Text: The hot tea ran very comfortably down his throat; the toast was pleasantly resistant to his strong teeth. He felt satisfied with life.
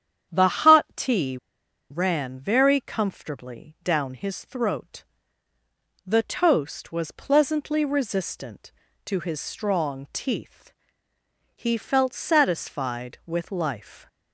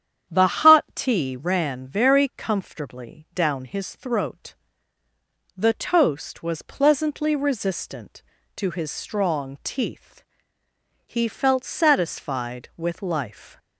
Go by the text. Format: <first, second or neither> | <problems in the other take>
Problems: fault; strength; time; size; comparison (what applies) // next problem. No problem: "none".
second | starts louder than the rest; strong; until 1.9 s; 9 dB; strong in the second // pauses between "tea" and "ran"; noticeable; at 1.3 s; 0.52 s long